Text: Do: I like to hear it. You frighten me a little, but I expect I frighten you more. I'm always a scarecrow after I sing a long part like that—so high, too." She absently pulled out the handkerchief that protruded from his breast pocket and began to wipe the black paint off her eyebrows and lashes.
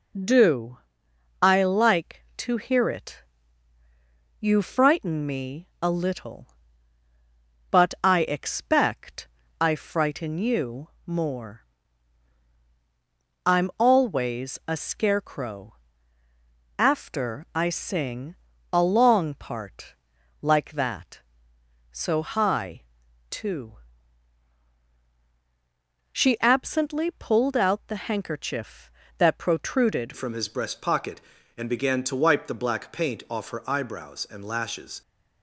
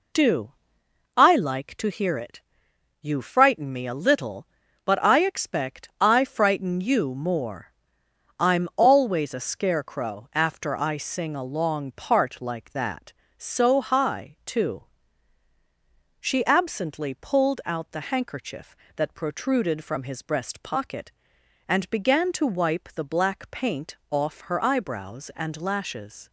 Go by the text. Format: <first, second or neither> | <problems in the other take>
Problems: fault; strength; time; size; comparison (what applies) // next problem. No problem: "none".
second | pauses between "expect" and "I"; slight; at 9.2 s; 0.32 s long // pauses between "you" and "more"; slight; at 10.8 s; 0.18 s long // pauses between "scarecrow" and "after"; at 15.7 s; 1.0 s long // pauses between "sing" and "a"; slight; at 18.3 s; 0.36 s long // pauses between "part" and "like"; noticeable; at 19.9 s; 0.48 s long // changes voice at "from"; from 30.1 s on; 4.9 s long